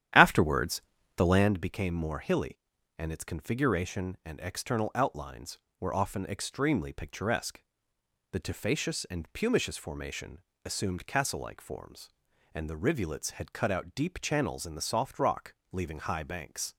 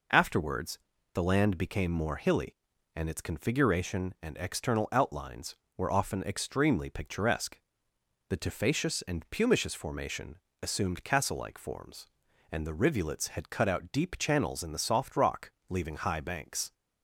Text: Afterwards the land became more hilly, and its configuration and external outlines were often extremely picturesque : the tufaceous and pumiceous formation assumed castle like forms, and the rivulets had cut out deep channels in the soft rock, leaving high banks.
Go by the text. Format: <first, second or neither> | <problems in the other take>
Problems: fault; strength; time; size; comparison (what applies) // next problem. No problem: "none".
second | starts louder than the rest; strong; until 1.5 s; 11 dB // pauses between "Afterwards" and "the"; slight; at 0.7 s; 0.36 s long; slight in the second // pauses between "formation" and "assumed"; slight; at 10.4 s; 0.22 s long; slight in the second